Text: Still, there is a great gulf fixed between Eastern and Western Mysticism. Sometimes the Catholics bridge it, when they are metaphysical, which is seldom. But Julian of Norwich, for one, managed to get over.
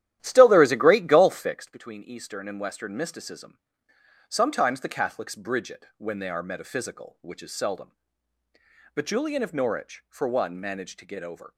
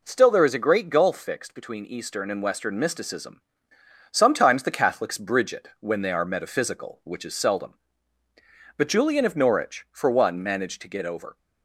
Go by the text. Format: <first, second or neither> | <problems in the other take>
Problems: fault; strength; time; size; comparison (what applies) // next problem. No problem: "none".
second | starts louder than the rest; strong; until 1.8 s; 12.5 dB